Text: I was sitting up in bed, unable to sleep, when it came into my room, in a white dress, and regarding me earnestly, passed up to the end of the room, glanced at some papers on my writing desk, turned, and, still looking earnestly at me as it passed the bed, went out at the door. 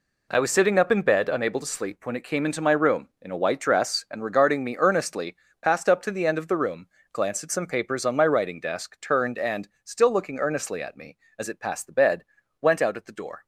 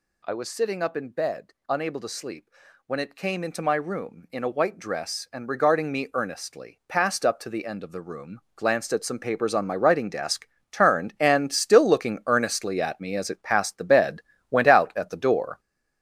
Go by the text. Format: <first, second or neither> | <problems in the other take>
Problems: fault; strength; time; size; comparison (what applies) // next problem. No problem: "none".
first | gets louder; throughout; 6.5 dB